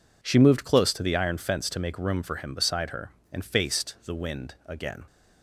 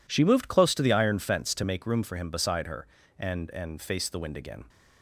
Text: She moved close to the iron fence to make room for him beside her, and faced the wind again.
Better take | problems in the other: first | says "and" twice; at 3.4 s

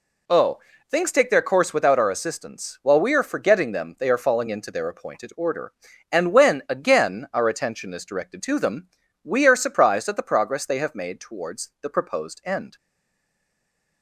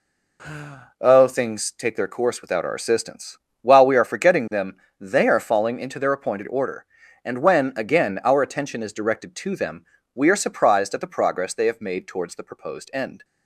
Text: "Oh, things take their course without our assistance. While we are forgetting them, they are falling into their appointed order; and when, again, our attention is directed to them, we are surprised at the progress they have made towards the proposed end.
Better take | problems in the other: second | stays silent after the last word; noticeable; from 12.7 s on; 1.3 s long

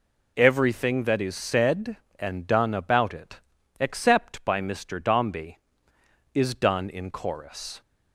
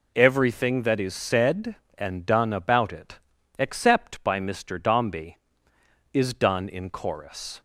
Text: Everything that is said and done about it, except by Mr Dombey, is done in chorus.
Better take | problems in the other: neither | none

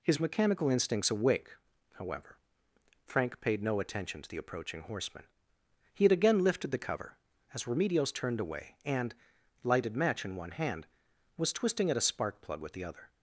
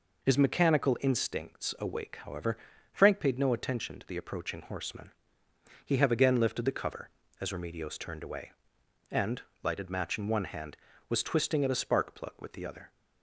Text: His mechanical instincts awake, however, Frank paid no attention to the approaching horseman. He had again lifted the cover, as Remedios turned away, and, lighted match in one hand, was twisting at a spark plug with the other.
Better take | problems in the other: first | says "have" for "had"; at 5.9 s

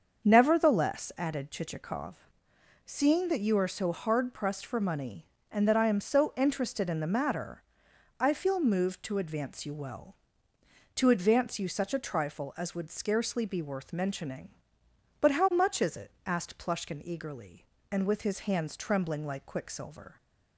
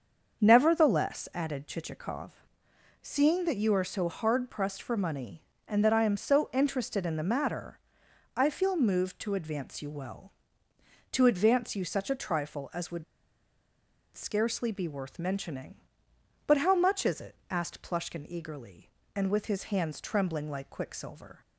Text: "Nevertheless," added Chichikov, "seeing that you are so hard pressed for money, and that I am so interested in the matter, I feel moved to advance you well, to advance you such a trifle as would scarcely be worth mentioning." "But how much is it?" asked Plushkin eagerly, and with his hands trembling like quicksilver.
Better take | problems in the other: first | starts louder than the rest; until 1.4 s; 6.5 dB; also in the first // pauses between "would" and "scarcely"; at 13.0 s; 1.1 s long

